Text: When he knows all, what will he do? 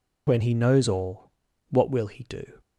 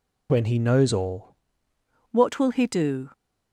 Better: first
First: none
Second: changes voice at "what"; from 2.1 s on; 1.0 s long

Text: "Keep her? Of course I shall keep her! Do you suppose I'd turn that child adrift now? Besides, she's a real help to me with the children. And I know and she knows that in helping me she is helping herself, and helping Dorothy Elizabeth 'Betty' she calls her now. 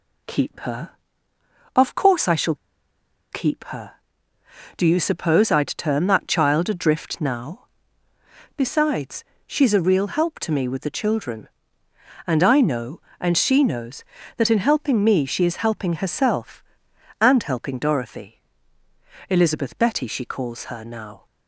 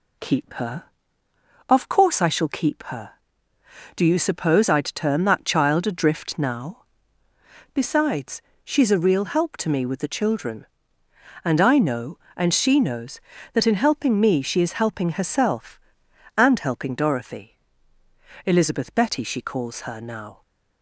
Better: second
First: pauses between "shall" and "keep"; noticeable; at 2.5 s; 0.77 s long // pauses between "Dorothy" and "Elizabeth"; noticeable; at 18.4 s; 0.88 s long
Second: pauses between "Dorothy" and "Elizabeth"; noticeable; at 17.5 s; 0.88 s long

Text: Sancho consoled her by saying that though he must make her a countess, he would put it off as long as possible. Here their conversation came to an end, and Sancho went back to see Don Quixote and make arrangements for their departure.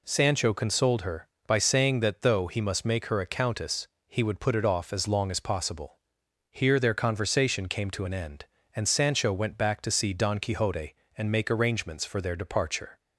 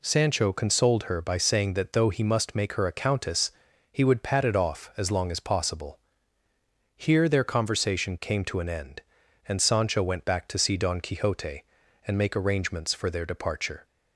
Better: first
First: none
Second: says "pat" for "put"; at 4.2 s

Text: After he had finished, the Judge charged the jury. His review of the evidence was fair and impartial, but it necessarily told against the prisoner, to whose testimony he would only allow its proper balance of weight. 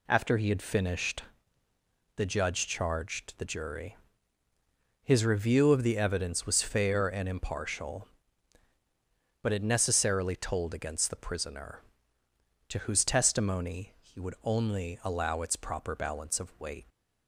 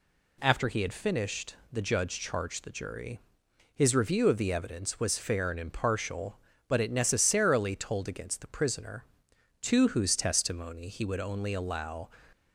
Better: first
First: none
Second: stops before "its proper balance of weight"; at 12.3 s

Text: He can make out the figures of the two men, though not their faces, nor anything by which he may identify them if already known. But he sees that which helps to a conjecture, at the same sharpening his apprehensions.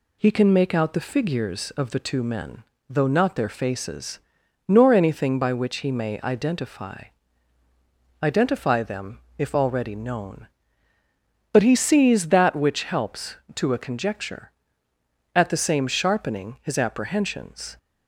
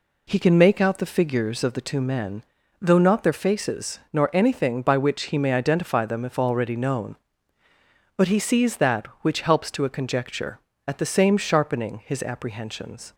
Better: second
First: says "identify" twice; at 8.2 s // pauses between "them" and "if"; slight; at 9.1 s; 0.18 s long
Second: none

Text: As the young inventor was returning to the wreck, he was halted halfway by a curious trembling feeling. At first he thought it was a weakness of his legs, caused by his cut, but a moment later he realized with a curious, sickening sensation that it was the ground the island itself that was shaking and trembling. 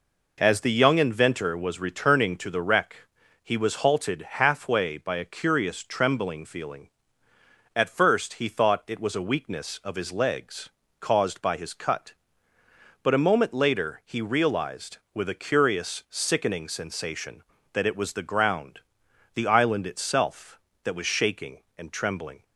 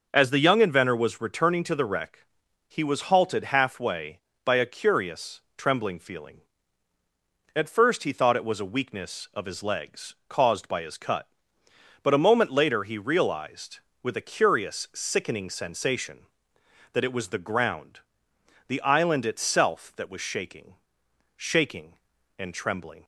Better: first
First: pauses between "ground" and "the"; noticeable; at 18.7 s; 0.56 s long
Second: pauses between "curious" and "trembling"; slight; at 5.3 s; 0.16 s long // pauses between "ground" and "the"; noticeable; at 17.9 s; 0.66 s long // says "shaking" twice; at 21.3 s

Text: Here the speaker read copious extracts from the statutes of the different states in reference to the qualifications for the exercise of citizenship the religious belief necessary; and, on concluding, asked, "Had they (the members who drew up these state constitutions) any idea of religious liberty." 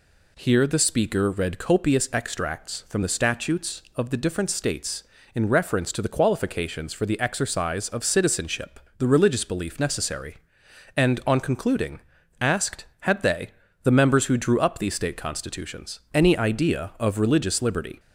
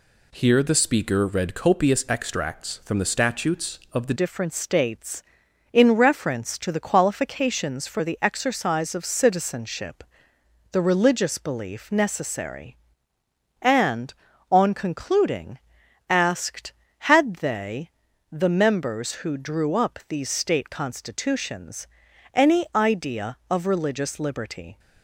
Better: first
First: pauses between "citizenship" and "the"; slight; at 8.7 s; 0.20 s long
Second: changes voice at "different"; from 4.1 s on; 20.6 s long // pauses between "citizenship" and "the"; noticeable; at 10.0 s; 0.70 s long

